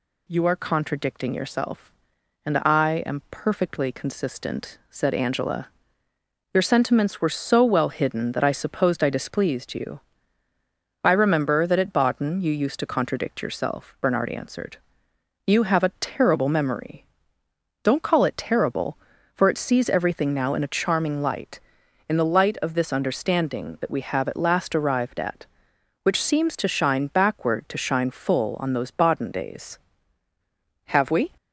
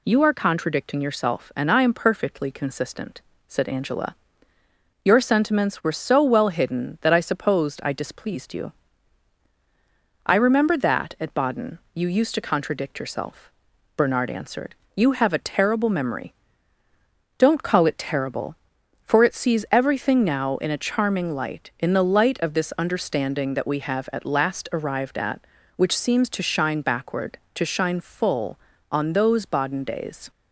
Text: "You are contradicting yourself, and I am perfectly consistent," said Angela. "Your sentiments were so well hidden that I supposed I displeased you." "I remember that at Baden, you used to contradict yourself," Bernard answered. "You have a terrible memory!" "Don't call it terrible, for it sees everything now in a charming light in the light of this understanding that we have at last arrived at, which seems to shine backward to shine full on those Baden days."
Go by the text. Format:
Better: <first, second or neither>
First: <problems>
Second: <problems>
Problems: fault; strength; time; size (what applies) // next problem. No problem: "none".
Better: second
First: goes on to say "Have we"; slight; from 30.8 s on; 0.46 s long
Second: none